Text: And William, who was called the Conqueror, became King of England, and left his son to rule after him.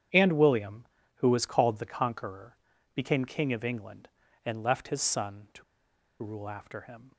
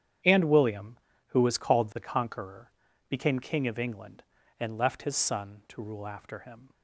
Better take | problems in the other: second | starts louder than the rest; strong; until 1.4 s; 9 dB; strong in the second // pauses between "to" and "rule"; noticeable; at 5.6 s; 0.59 s long

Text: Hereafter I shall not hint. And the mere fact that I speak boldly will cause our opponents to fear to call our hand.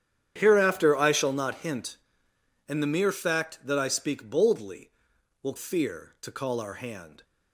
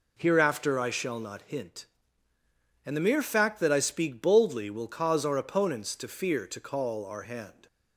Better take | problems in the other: second | starts louder than the rest; strong; until 1.3 s; 9.5 dB // skips "cause our opponents to"; at 5.5 s

